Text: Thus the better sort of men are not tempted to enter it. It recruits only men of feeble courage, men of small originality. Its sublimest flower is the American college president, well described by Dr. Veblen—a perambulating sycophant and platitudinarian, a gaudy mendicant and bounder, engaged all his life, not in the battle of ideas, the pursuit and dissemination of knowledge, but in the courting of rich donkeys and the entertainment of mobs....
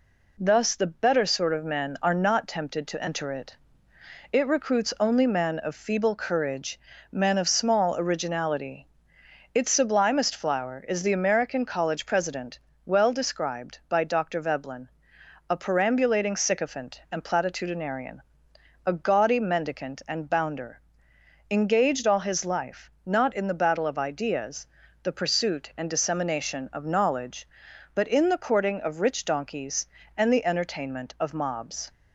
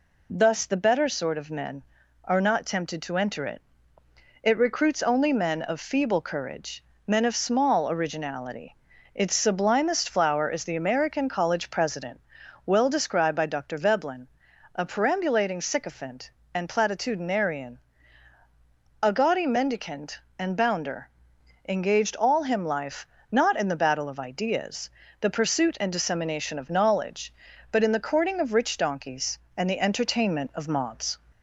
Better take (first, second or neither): first